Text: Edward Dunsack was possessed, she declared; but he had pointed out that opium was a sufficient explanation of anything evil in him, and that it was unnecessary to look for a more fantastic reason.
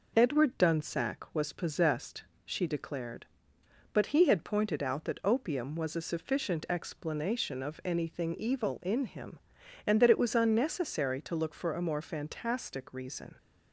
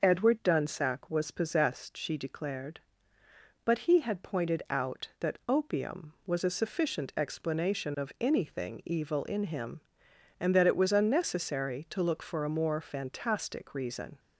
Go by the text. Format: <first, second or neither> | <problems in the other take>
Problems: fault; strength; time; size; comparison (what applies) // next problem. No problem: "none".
neither | none